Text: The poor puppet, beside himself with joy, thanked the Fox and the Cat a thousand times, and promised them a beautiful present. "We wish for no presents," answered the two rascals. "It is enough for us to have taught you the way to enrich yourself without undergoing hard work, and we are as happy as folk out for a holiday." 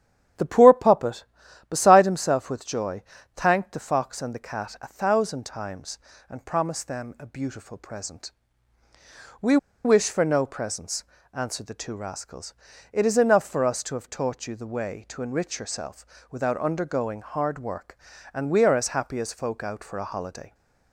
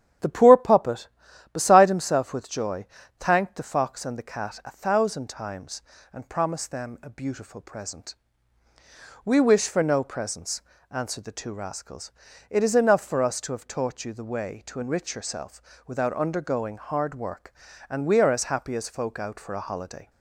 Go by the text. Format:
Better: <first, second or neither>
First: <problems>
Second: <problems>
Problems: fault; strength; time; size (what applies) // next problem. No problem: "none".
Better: second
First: starts louder than the rest; strong; until 1.8 s; 9.5 dB // pauses between "We" and "wish"; slight; at 9.5 s; 0.28 s long // pauses between "yourself" and "without"; slight; at 16.0 s; 0.24 s long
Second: starts louder than the rest; strong; until 1.6 s; 9.5 dB // pauses between "yourself" and "without"; slight; at 15.6 s; 0.24 s long